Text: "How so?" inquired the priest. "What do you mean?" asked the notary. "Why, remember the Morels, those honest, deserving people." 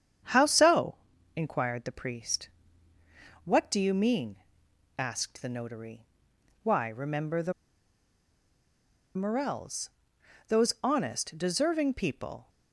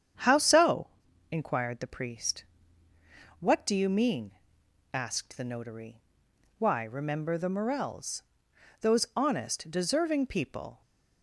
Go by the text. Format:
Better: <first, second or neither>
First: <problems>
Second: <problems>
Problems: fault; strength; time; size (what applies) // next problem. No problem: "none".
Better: second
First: starts louder than the rest; strong; until 1.6 s; 8.5 dB // pauses between "the" and "Morels"; strong; at 7.5 s; 1.6 s long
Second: starts louder than the rest; strong; until 1.6 s; 8.5 dB